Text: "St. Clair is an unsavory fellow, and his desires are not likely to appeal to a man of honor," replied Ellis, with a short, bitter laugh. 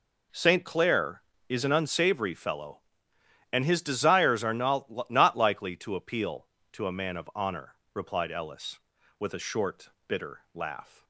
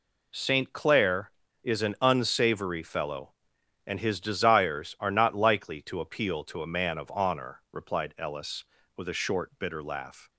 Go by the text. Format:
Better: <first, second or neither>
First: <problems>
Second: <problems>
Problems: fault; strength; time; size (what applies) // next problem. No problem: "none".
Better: second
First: says "not" twice; at 5.0 s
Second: none